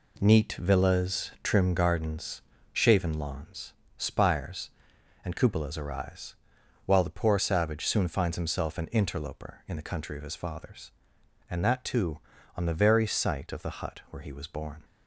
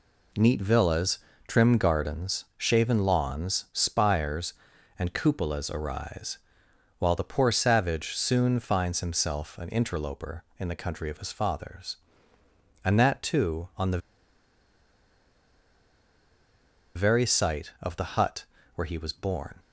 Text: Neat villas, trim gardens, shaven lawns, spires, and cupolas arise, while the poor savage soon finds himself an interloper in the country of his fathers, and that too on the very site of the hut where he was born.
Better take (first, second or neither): first